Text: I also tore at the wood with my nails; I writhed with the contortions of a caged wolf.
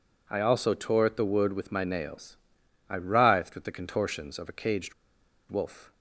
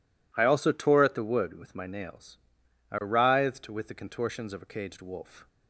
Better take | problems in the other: second | pauses between "caged" and "wolf"; noticeable; at 4.9 s; 0.56 s long

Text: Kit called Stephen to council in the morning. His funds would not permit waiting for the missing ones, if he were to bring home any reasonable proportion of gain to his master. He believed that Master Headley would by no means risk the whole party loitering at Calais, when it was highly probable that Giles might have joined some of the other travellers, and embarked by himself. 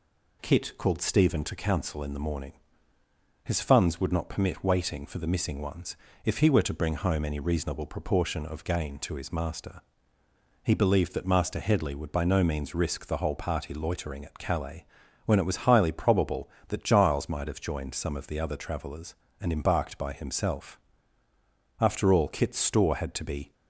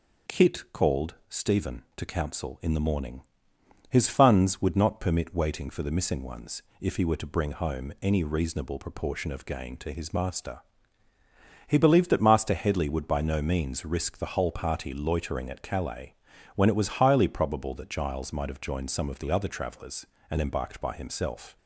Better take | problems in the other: second | goes on to say "After all Kit's store had to be"; strong; from 21.7 s on; 1.7 s long

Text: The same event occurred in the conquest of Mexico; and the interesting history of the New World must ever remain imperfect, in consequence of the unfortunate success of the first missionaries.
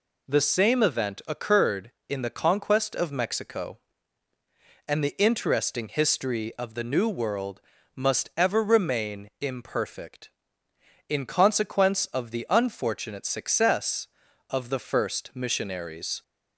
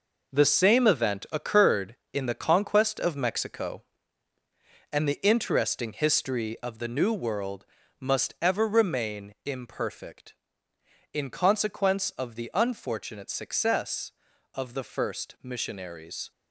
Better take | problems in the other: first | gets quieter; strong; throughout; 8 dB // pauses between "World" and "must"; slight; at 7.6 s; 0.34 s long; slight in the first

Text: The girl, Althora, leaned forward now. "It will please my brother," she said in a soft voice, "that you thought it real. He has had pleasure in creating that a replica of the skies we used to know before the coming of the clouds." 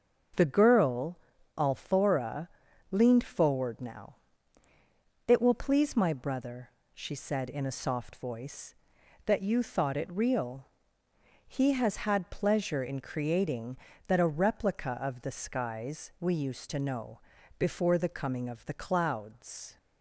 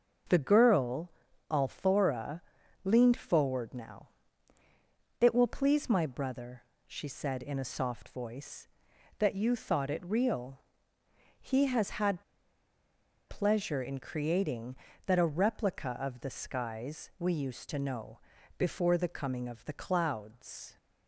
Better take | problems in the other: first | starts louder than the rest; until 1.7 s; 6.5 dB; also in the first // pauses between "had" and "pleasure"; at 12.2 s; 1.0 s long // pauses between "know" and "before"; at 18.1 s; 0.40 s long; also in the first

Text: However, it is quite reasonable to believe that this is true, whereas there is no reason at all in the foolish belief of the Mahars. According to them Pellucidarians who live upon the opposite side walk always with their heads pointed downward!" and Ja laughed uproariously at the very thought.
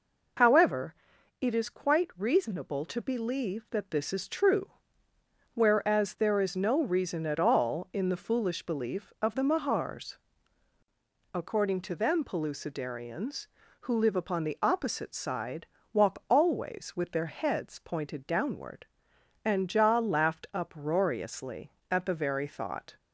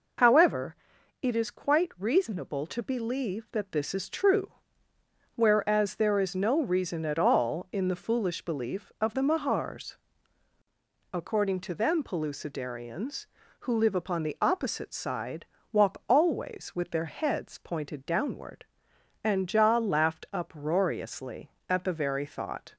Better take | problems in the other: neither | pauses between "side" and "walk"; slight; the same in both

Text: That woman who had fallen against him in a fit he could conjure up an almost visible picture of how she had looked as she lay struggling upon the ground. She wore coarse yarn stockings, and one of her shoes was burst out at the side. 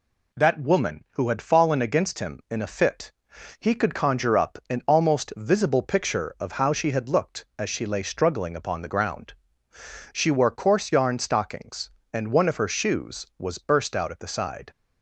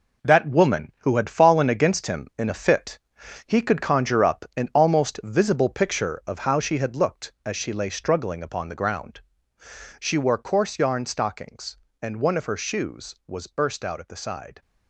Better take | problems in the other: first | gets quieter; strong; throughout; 8.5 dB // pauses between "fit" and "he"; noticeable; at 2.9 s; 0.48 s long; noticeable in the first

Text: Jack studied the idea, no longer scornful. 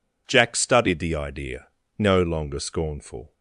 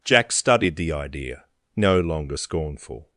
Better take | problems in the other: neither | none

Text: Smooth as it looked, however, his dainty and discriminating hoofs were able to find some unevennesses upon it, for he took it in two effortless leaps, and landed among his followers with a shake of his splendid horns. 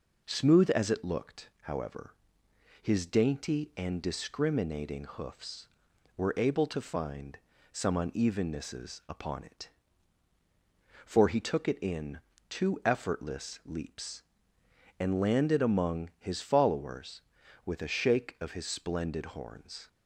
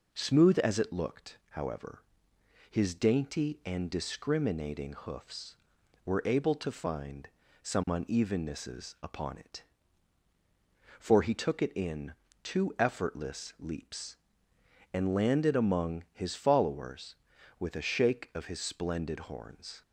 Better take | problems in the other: neither | pauses between "find" and "some"; slight; the same in both // pauses between "in" and "two"; slight; the same in both

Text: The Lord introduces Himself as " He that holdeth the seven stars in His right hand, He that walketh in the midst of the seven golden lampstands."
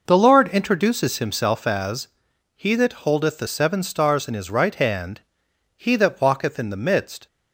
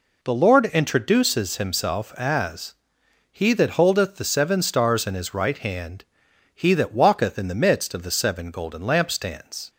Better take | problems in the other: second | stops before "of the seven golden lampstands"; at 7.2 s

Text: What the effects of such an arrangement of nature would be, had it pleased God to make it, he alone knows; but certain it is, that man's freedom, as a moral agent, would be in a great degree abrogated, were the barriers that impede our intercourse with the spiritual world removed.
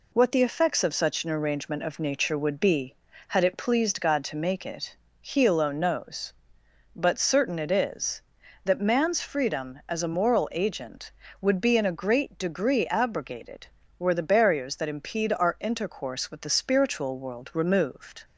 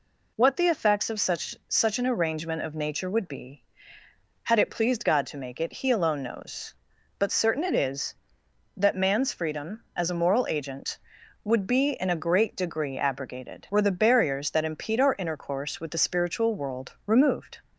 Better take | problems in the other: first | says "such" twice; at 1.6 s

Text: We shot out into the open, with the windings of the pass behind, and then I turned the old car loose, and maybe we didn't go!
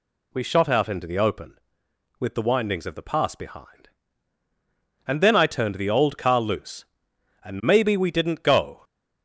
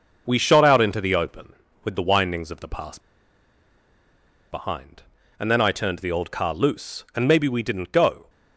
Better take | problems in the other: first | pauses between "pass" and "behind"; strong; at 2.9 s; 1.5 s long

